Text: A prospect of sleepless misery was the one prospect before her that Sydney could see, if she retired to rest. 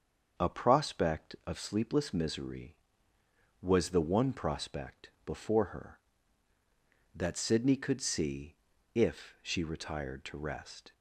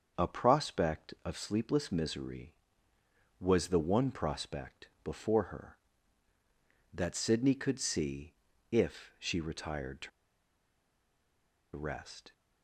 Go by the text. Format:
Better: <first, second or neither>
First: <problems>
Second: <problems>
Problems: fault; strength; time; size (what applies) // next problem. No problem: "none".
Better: first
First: starts louder than the rest; until 1.4 s; 6.5 dB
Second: starts louder than the rest; until 1.2 s; 6.5 dB // pauses between "to" and "rest"; strong; at 10.1 s; 1.6 s long